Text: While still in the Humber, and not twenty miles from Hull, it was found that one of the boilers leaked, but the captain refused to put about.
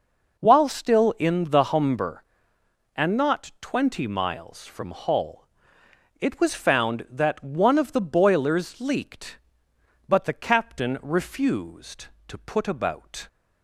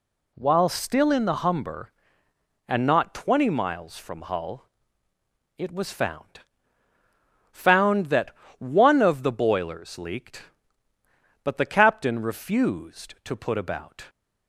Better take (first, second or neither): first